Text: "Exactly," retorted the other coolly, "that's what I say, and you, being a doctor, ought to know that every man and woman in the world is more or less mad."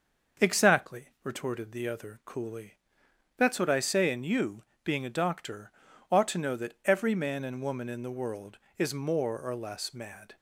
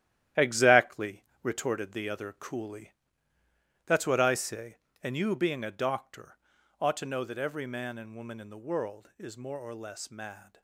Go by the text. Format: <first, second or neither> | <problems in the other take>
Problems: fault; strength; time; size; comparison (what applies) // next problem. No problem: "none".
first | gets quieter; strong; throughout; 8.5 dB // starts louder than the rest; strong; until 1.5 s; 12 dB; also in the first